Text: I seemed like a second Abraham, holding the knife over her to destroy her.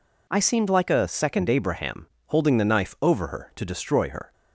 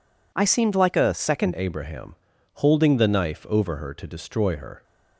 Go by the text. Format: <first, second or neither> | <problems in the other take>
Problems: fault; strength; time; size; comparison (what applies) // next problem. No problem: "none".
first | changes voice at "Abraham"; from 1.5 s on; 3.3 s long